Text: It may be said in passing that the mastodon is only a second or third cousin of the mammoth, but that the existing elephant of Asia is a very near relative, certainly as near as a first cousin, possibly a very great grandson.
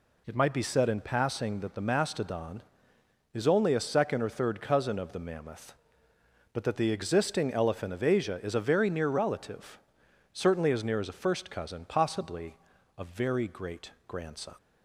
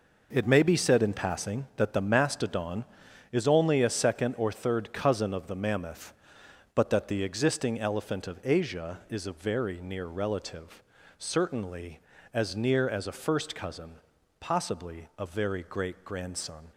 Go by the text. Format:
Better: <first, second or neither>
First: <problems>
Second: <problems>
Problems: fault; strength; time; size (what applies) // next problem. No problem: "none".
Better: second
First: says "might" for "may"; at 0.3 s // pauses between "possibly" and "a"; at 12.5 s; 0.40 s long // pauses between "great" and "grandson"; slight; at 13.8 s; 0.18 s long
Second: none